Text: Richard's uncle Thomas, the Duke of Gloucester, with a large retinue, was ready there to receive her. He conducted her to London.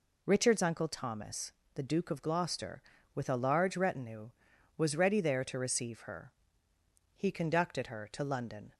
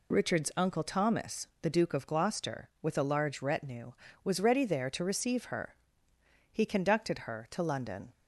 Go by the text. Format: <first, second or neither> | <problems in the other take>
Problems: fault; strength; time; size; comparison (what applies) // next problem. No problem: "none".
neither | none